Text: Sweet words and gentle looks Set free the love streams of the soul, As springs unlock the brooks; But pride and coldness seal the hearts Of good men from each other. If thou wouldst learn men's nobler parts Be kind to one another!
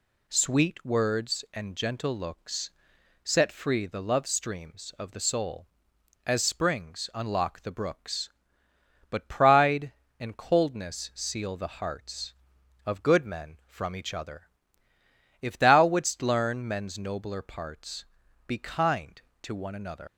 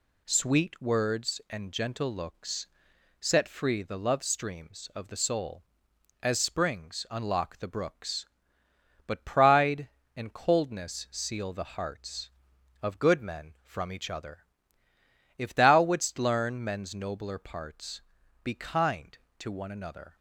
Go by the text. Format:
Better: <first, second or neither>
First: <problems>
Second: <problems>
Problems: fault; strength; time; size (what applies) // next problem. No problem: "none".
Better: second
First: pauses between "looks" and "Set"; noticeable; at 2.7 s; 0.52 s long // pauses between "parts" and "Be"; at 18.0 s; 0.44 s long // leaves "another" unfinished; at 20.0 s; 120 ms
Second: pauses between "looks" and "Set"; noticeable; at 2.6 s; 0.52 s long // pauses between "parts" and "Be"; at 17.9 s; 0.44 s long